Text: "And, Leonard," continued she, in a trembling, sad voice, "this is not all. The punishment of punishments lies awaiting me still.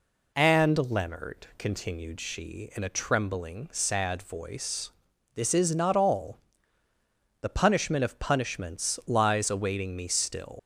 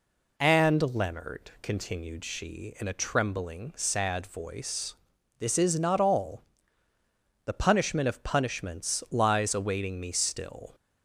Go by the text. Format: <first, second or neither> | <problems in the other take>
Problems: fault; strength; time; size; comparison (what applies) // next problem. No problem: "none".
second | leaves "still" unfinished; at 10.5 s; 110 ms